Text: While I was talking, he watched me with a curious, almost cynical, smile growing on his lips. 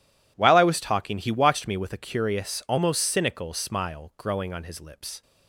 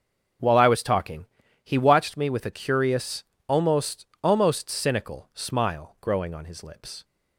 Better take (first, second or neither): first